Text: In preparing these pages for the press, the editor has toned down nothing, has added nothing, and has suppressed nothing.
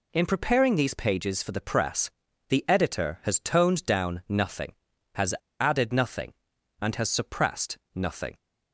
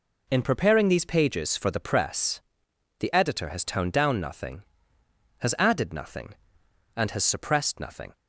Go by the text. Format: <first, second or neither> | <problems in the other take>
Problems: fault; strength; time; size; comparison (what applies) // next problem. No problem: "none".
second | pauses between "has" and "added"; slight; at 5.3 s; 0.25 s long // pauses between "suppressed" and "nothing"; slight; at 7.7 s; 0.18 s long